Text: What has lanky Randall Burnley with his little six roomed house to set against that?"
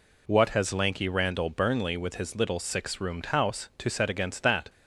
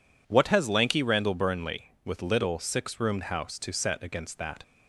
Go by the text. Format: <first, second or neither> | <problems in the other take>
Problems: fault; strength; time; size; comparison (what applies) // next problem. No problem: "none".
first | skips "his"; at 2.2 s